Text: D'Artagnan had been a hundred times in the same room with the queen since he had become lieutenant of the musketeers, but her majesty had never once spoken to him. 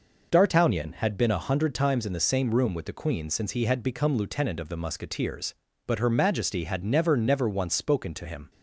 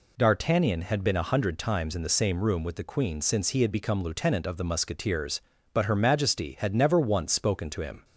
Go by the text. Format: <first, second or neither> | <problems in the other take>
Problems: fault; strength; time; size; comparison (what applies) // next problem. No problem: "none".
second | says "never" twice; at 7.1 s